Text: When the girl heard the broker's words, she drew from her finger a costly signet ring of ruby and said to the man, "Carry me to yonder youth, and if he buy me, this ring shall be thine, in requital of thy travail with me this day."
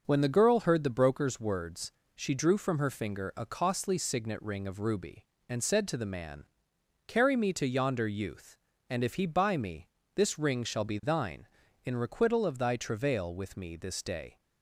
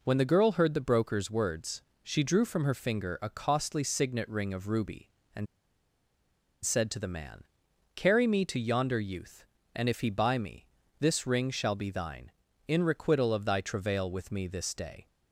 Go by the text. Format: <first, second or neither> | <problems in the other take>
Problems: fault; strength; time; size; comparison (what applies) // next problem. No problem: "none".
first | pauses between "and" and "said"; at 5.4 s; 1.1 s long